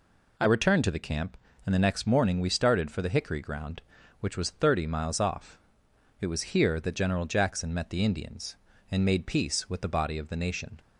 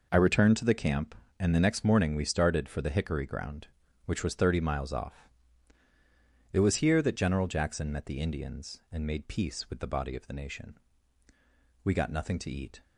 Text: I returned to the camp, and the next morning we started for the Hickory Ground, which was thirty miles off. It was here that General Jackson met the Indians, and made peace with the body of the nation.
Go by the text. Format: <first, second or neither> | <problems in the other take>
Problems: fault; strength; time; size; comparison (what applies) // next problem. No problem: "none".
first | goes on to say "We got nothing to eat"; noticeable; from 11.8 s on; 0.98 s long